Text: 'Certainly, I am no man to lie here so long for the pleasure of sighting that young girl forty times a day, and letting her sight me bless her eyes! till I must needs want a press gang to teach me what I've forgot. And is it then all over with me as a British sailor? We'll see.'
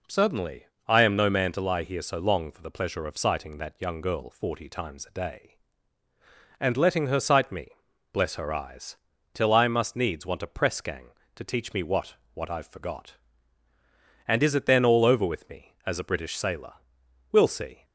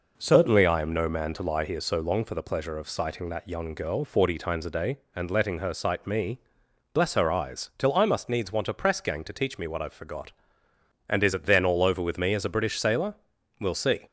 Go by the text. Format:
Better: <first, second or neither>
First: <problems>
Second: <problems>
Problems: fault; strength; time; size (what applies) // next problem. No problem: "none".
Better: second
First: pauses between "me" and "bless"; at 7.6 s; 0.44 s long // says "what" twice; at 12.3 s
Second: pauses between "me" and "bless"; noticeable; at 6.3 s; 0.54 s long